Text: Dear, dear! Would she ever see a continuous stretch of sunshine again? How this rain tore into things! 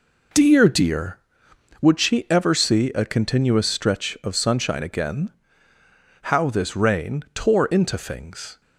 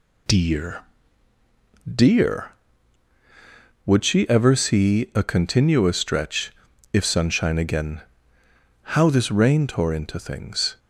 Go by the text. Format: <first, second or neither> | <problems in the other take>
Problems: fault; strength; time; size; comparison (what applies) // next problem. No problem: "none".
first | says "if" for "of"; at 6.9 s